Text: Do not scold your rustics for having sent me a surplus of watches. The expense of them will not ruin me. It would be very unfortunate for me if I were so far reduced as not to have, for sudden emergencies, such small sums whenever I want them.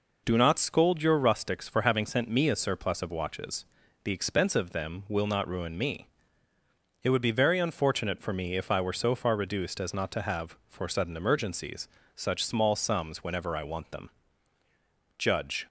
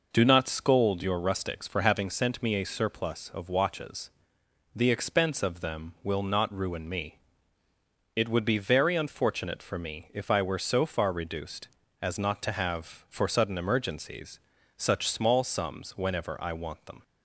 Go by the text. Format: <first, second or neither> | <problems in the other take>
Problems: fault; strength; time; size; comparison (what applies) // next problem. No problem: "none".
second | goes on to say "Judge"; slight; from 15.1 s on; 0.48 s long